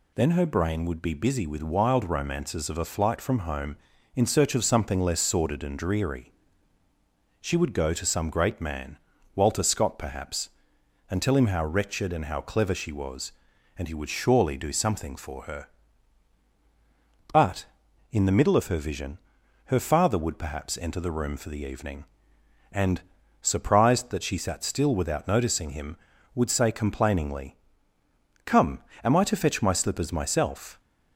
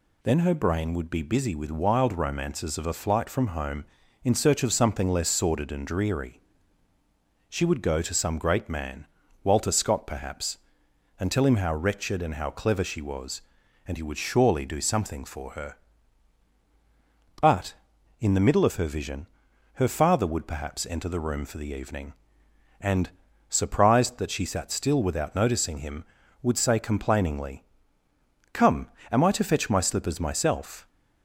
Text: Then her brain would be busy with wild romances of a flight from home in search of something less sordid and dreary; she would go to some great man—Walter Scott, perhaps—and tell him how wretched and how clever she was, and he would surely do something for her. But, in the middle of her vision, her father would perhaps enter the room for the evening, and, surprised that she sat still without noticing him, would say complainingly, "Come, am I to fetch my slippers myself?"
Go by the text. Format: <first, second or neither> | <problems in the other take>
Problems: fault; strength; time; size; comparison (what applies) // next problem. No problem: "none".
neither | none